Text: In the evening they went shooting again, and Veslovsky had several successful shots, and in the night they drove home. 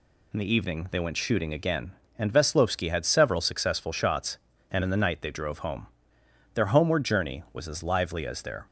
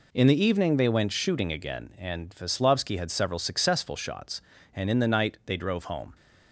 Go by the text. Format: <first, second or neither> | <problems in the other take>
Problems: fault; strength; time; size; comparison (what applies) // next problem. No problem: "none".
second | goes on to say "Their homeward journey was as lively as their"; strong; from 6.5 s on; 2.1 s long